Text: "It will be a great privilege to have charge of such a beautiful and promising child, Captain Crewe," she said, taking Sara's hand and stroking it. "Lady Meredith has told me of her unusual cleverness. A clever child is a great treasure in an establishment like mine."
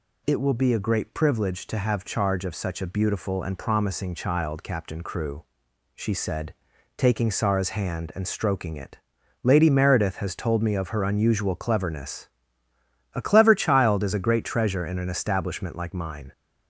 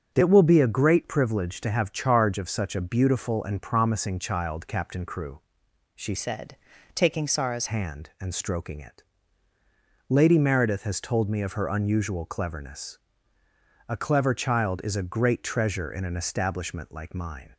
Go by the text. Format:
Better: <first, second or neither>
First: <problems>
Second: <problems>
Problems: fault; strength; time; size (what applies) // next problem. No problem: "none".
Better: first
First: none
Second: starts louder than the rest; strong; until 1.1 s; 8 dB // changes voice from "said" to "Sara's"; from 6.1 to 7.6 s; 1.5 s long